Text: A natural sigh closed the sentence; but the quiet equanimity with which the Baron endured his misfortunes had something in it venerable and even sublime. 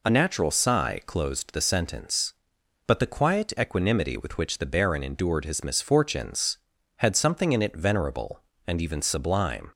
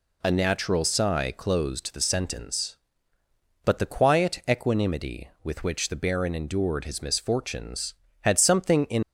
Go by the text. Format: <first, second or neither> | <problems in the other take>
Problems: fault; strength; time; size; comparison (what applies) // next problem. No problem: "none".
first | stops before "it venerable and even sublime"; at 9.0 s